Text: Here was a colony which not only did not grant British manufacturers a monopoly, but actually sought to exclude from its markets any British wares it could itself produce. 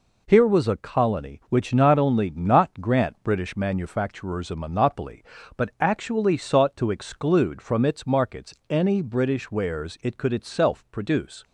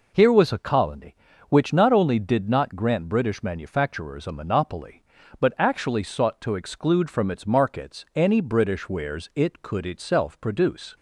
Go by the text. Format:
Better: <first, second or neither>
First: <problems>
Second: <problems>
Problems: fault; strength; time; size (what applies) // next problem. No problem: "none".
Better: second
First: skips "did"; at 2.2 s // pauses between "markets" and "any"; slight; at 8.5 s; 0.16 s long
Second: none